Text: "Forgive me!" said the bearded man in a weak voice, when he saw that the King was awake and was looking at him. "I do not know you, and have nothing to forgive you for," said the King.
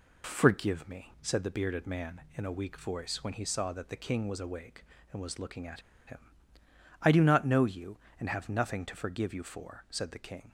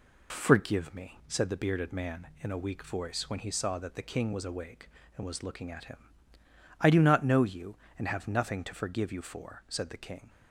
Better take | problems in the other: second | pauses between "at" and "him"; slight; at 5.8 s; 0.25 s long

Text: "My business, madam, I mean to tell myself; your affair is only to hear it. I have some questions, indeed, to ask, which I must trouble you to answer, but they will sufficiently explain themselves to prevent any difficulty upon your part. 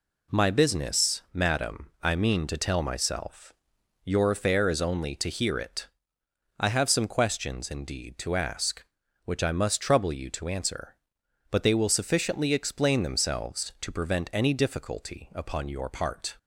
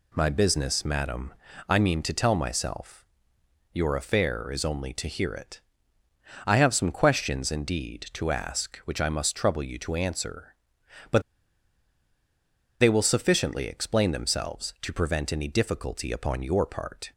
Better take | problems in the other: first | pauses between "but" and "they"; strong; at 11.2 s; 1.5 s long

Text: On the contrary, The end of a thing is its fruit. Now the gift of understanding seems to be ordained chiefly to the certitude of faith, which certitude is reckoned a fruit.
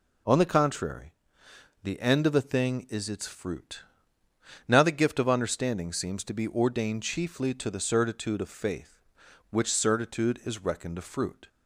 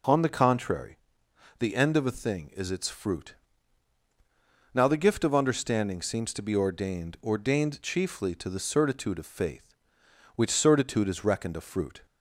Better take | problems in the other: first | says "ordained" twice; at 7.2 s

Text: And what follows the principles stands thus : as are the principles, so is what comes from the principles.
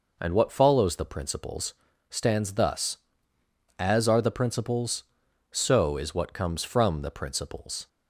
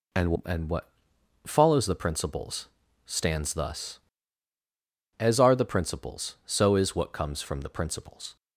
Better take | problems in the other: first | says "And" twice; at 0.4 s // pauses between "what" and "follows"; noticeable; at 0.8 s; 0.58 s long // pauses between "principles" and "stands"; at 2.6 s; 0.38 s long; slight in the first

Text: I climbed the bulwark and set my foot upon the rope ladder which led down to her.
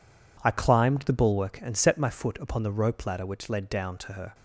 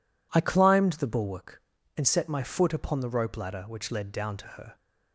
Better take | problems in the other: second | gets quieter; strong; throughout; 11.5 dB

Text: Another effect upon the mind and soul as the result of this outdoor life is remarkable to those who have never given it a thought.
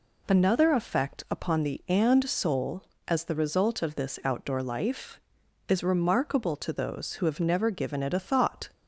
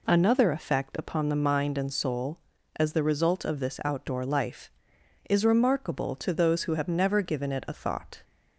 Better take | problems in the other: second | skips "mind"; at 1.8 s

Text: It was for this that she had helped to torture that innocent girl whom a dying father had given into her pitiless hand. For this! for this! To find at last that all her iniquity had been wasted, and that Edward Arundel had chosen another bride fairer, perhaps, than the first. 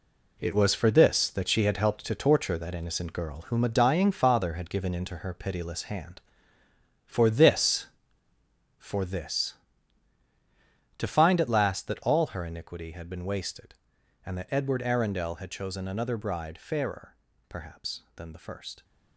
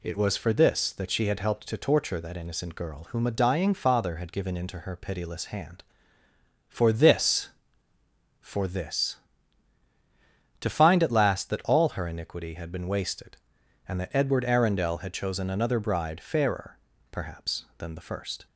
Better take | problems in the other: second | gets quieter; strong; throughout; 8.5 dB

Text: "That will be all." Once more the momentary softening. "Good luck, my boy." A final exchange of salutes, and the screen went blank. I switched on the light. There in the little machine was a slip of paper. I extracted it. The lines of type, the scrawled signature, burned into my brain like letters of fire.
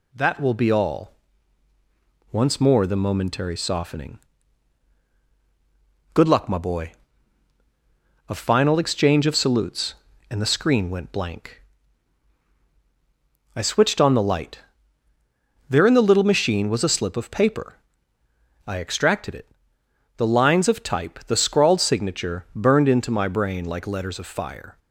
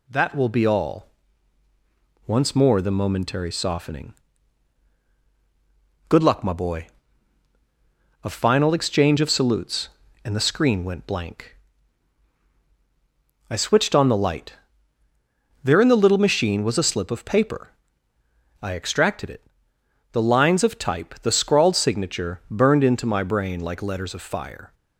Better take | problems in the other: neither | none

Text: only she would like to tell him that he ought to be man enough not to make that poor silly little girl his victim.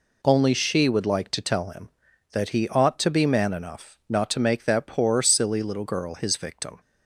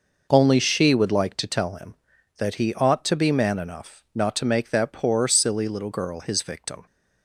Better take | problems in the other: first | starts louder than the rest; noticeable; until 1.3 s; 5.5 dB

